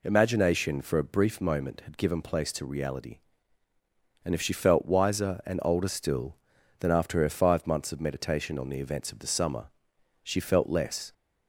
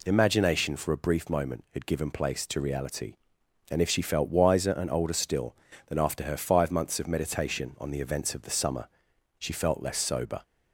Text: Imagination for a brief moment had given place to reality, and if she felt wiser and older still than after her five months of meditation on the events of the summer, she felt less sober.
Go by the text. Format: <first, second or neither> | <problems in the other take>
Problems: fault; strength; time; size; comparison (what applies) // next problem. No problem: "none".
second | stops before "sober"; at 11.1 s